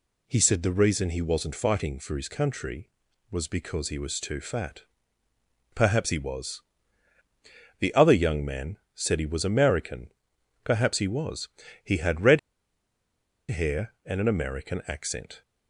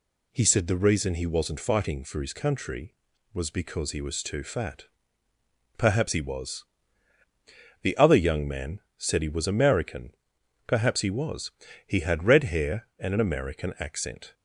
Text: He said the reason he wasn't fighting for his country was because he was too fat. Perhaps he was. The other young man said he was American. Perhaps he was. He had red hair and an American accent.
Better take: second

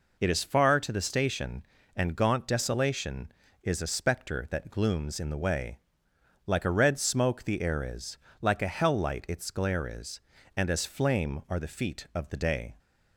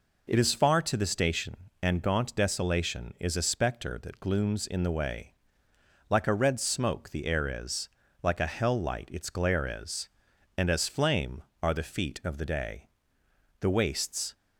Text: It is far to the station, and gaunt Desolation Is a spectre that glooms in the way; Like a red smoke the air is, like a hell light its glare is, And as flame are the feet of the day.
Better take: first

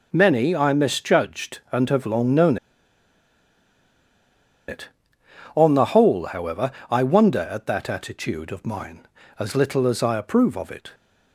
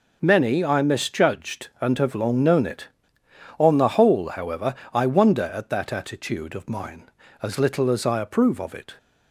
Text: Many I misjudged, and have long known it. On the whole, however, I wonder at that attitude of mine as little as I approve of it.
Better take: second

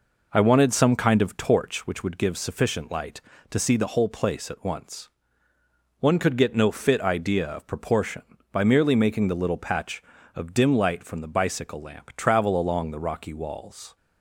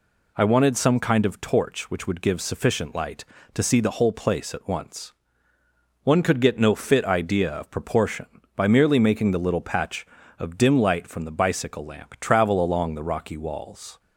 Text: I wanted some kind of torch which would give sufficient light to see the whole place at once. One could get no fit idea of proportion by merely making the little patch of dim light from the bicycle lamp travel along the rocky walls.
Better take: second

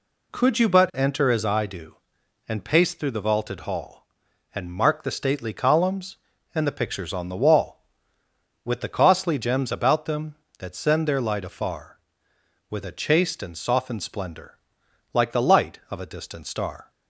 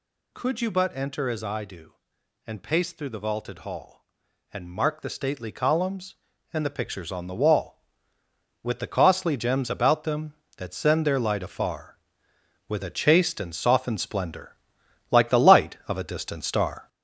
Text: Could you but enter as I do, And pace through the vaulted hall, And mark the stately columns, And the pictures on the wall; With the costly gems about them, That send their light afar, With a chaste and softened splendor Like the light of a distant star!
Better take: first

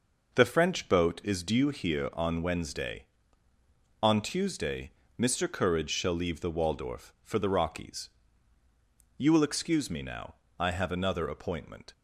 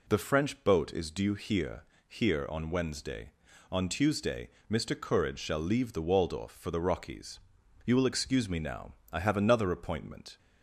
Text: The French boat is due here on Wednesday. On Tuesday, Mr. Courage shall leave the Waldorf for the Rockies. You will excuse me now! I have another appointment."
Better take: first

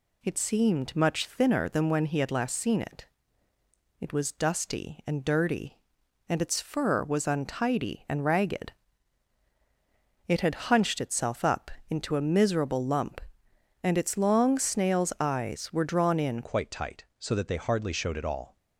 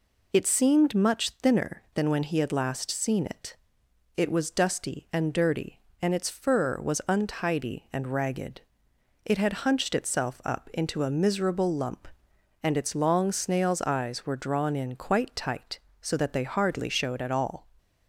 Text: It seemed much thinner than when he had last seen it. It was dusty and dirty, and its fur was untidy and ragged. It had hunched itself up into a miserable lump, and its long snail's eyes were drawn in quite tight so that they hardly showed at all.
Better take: second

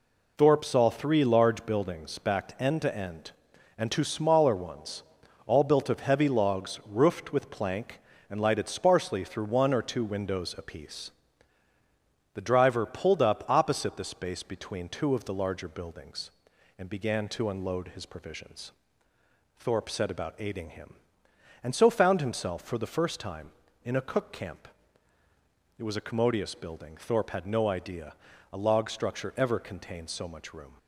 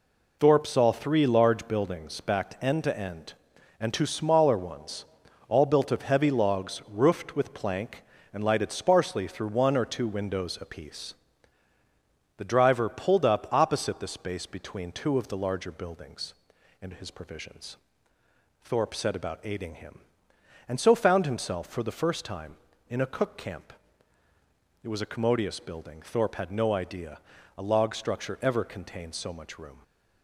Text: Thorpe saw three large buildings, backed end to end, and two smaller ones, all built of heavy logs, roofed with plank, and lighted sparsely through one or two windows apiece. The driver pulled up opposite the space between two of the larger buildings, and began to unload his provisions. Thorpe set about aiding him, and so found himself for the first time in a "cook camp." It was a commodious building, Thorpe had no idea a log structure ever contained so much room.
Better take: first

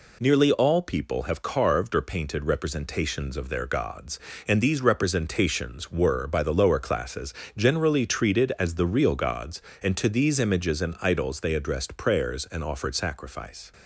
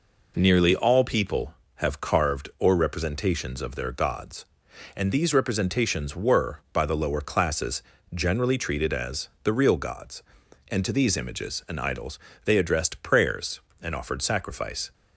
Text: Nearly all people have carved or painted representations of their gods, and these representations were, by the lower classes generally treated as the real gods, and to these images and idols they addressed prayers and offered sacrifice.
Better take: first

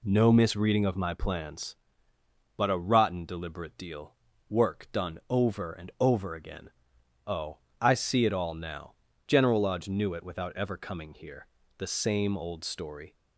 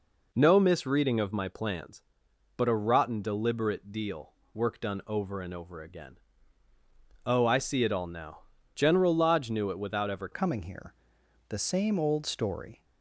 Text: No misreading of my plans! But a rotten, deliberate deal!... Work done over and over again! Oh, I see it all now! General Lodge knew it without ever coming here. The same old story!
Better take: first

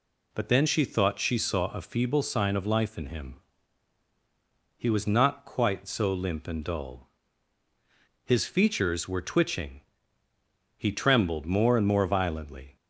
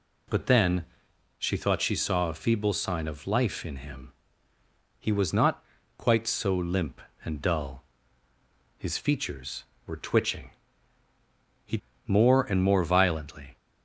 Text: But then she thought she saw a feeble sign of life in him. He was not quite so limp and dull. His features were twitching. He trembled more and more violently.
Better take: first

